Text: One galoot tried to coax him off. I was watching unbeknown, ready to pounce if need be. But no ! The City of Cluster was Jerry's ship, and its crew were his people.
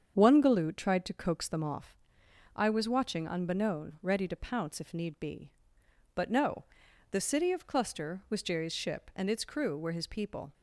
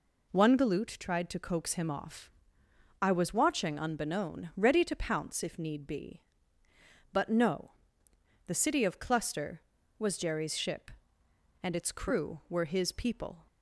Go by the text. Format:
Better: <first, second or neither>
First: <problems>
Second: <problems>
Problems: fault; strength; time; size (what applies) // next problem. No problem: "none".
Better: second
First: starts louder than the rest; strong; until 1.1 s; 7.5 dB // says "them" for "him"; at 1.4 s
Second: none